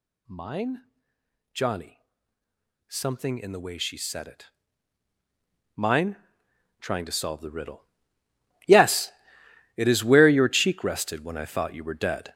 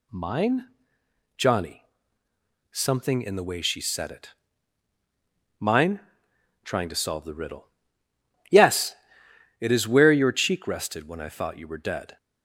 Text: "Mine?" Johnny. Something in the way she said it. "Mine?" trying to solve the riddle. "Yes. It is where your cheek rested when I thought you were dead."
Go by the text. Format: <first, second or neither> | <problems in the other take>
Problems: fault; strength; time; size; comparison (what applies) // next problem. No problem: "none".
second | gets louder; strong; throughout; 8.5 dB